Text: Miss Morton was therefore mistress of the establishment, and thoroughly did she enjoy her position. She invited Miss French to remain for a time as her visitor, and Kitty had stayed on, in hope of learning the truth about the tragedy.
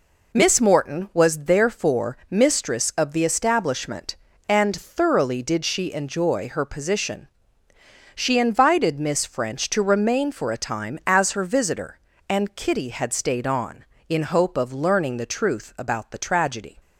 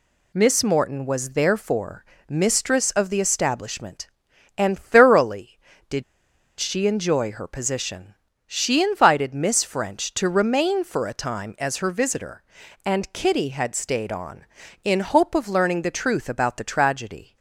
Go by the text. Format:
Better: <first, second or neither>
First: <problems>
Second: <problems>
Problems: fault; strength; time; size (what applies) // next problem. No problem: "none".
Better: first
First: none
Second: pauses between "therefore" and "mistress"; slight; at 2.0 s; 0.22 s long // pauses between "did" and "she"; noticeable; at 6.0 s; 0.56 s long